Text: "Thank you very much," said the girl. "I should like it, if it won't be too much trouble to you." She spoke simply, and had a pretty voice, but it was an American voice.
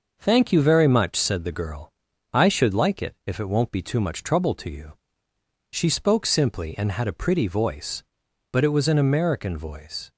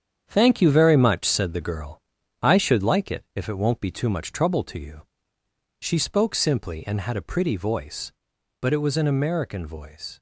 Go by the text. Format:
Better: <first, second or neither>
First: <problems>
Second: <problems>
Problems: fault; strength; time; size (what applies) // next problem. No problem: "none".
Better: first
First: none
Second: gets quieter; strong; throughout; 8 dB